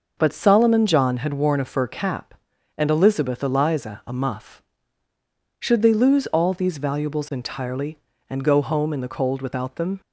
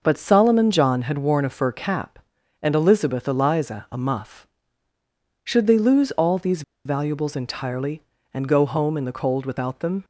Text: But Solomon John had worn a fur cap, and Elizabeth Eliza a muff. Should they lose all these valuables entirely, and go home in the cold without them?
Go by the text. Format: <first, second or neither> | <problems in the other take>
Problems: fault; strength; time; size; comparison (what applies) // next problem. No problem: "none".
first | pauses between "these" and "valuables"; slight; at 6.6 s; 0.24 s long